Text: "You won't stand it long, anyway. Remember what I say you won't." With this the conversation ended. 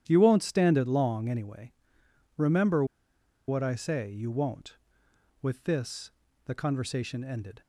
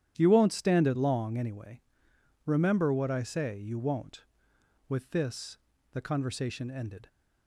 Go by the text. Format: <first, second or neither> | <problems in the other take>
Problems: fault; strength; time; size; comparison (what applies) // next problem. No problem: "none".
second | starts louder than the rest; strong; until 1.0 s; 10.5 dB; strong in the second // pauses between "Remember" and "what"; noticeable; at 2.8 s; 0.63 s long // pauses between "this" and "the"; slight; at 6.1 s; 0.32 s long; slight in the second